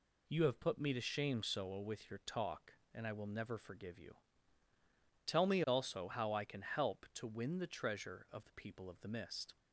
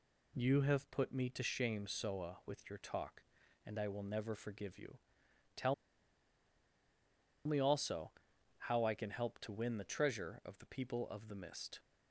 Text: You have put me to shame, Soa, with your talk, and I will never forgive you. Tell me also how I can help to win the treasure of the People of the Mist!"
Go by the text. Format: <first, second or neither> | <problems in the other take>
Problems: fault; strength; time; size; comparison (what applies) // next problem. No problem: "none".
first | pauses between "Tell" and "me"; strong; at 5.7 s; 1.7 s long // pauses between "also" and "how"; noticeable; at 8.1 s; 0.48 s long